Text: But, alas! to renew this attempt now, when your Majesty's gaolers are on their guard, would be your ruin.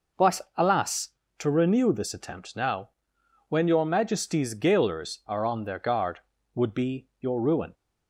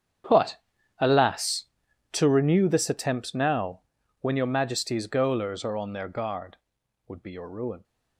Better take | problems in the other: first | gets quieter; strong; throughout; 16.5 dB

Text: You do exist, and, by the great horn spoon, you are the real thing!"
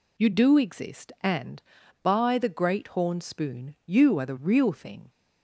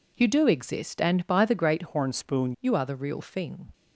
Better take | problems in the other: first | changes voice from "horn" to "spoon"; from 1.8 to 2.5 s; 0.7 s long

